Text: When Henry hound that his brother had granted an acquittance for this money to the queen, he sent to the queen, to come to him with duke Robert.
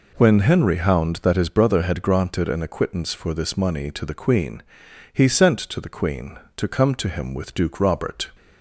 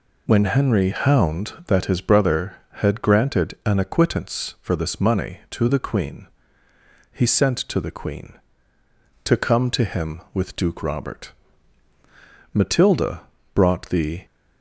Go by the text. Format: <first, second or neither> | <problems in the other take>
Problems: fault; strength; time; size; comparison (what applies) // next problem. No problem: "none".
first | goes on to say "Matilda brought the"; strong; from 12.5 s on; 1.7 s long